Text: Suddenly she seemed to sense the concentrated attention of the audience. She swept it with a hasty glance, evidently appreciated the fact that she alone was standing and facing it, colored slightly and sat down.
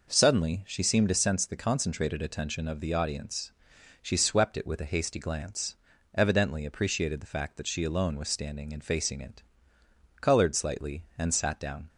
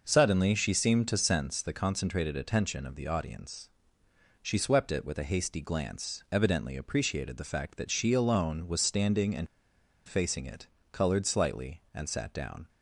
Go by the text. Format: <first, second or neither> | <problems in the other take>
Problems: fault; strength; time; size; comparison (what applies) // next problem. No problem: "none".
first | pauses between "and" and "facing"; noticeable; at 9.4 s; 0.61 s long